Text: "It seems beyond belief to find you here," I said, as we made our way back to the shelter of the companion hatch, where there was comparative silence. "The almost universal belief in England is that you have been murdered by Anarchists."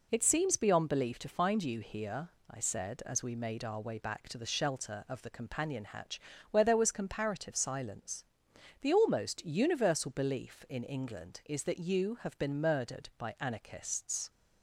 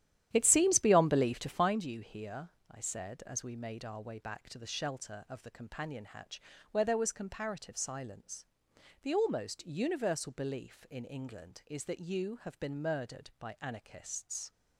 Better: first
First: none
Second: starts louder than the rest; strong; until 1.8 s; 11.5 dB

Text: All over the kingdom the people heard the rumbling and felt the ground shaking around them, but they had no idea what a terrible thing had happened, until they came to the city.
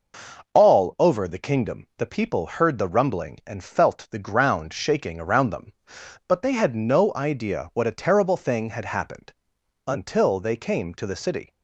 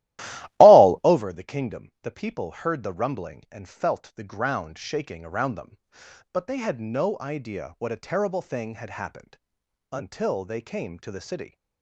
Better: first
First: none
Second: starts louder than the rest; strong; until 1.3 s; 15.5 dB

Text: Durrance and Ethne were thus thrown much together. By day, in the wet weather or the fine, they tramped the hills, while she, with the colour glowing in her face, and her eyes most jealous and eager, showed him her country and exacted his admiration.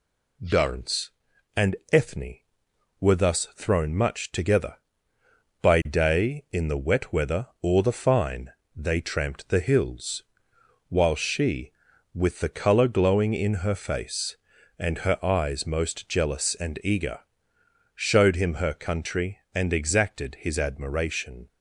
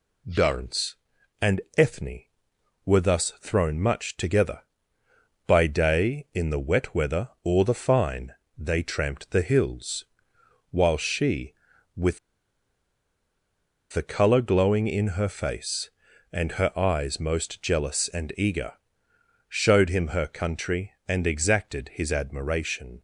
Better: first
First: pauses between "and" and "Ethne"; slight; at 1.7 s; 0.16 s long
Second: pauses between "and" and "Ethne"; slight; at 1.5 s; 0.16 s long // pauses between "with" and "the"; strong; at 12.1 s; 1.7 s long

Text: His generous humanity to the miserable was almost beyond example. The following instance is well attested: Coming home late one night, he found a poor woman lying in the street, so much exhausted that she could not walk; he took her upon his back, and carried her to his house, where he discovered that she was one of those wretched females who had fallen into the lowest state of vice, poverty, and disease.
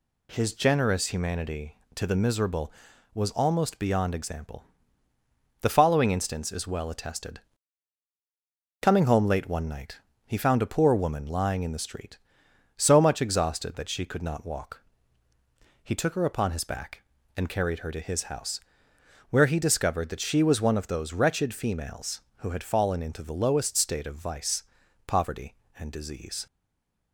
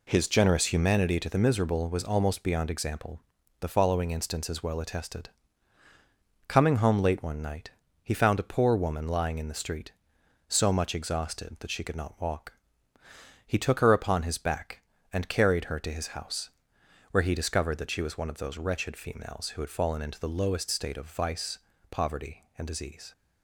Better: second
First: stays silent after the last word; slight; from 26.4 s on; 0.7 s long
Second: none

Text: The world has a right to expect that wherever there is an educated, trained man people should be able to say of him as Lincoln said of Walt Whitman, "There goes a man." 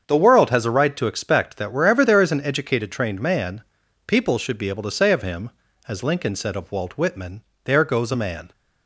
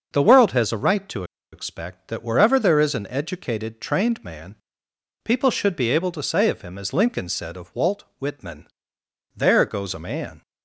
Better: first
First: starts louder than the rest; strong; until 1.1 s; 7 dB // pauses between "man" and "people"; at 3.6 s; 0.44 s long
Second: starts louder than the rest; until 1.1 s; 6 dB // pauses between "to" and "expect"; slight; at 1.2 s; 0.29 s long // pauses between "man" and "people"; noticeable; at 4.5 s; 0.70 s long

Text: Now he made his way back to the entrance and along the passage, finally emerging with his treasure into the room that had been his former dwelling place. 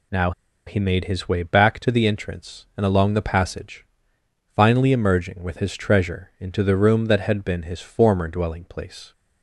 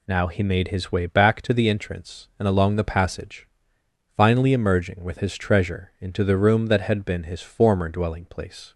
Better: second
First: pauses between "Now" and "he"; slight; at 0.3 s; 0.35 s long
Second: none

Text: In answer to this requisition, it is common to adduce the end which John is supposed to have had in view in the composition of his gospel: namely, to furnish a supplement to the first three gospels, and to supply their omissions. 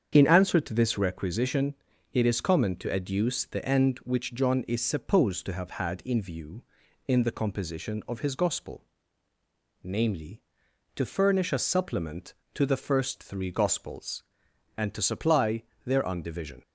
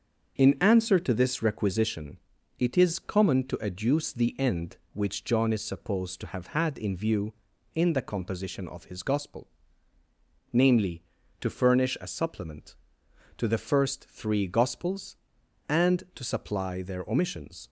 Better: second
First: starts louder than the rest; strong; until 1.1 s; 7.5 dB // pauses between "supply" and "their"; slight; at 15.6 s; 0.20 s long // says "undivision" for "omissions"; at 16.0 s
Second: starts louder than the rest; until 1.4 s; 6.5 dB

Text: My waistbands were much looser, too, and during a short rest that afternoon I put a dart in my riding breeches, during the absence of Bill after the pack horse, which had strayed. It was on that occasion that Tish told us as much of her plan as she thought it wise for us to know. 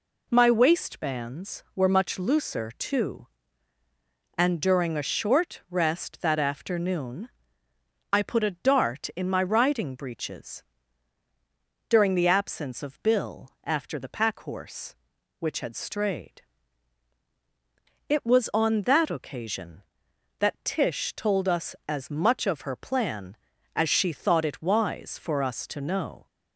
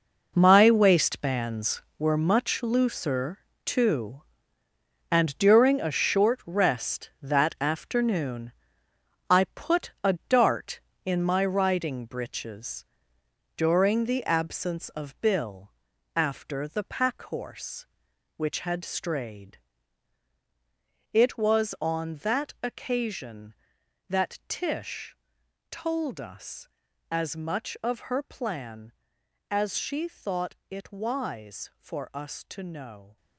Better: first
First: pauses between "afternoon" and "I"; noticeable; at 7.2 s; 0.84 s long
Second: gets quieter; strong; throughout; 11.5 dB // pauses between "afternoon" and "I"; noticeable; at 8.5 s; 0.80 s long // pauses between "Bill" and "after"; noticeable; at 15.7 s; 0.46 s long // pauses between "Tish" and "told"; noticeable; at 25.1 s; 0.56 s long

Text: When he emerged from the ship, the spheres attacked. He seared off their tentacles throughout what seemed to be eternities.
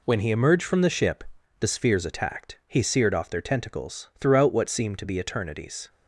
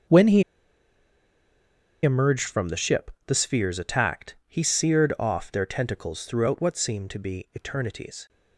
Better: first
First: none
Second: starts louder than the rest; until 2.6 s; 6.5 dB // pauses between "he" and "emerged"; strong; at 0.4 s; 1.6 s long

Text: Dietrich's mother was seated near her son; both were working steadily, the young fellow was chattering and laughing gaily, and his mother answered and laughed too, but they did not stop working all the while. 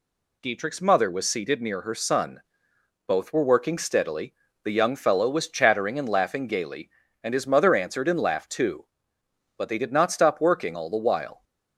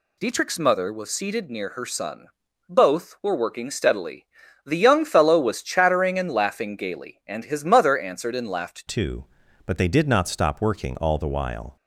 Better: first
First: none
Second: changes voice at "too"; from 8.8 s on; 2.9 s long

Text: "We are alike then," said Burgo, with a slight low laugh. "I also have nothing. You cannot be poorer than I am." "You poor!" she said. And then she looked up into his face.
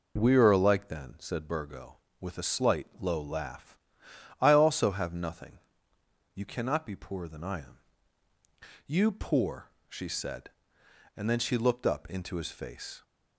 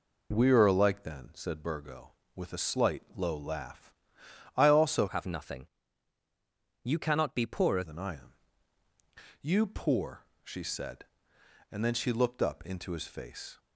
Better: first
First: pauses between "slight" and "low"; slight; at 2.8 s; 0.16 s long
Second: pauses between "slight" and "low"; slight; at 3.0 s; 0.16 s long // changes voice from "have" to "poorer"; from 5.0 to 7.8 s; 2.8 s long

